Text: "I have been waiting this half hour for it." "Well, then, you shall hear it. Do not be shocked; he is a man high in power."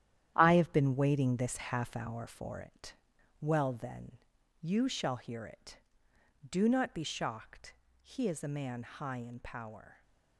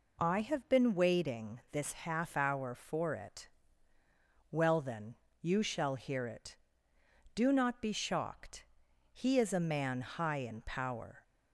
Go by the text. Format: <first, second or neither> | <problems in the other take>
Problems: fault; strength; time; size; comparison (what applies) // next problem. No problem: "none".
second | gets quieter; strong; throughout; 8.5 dB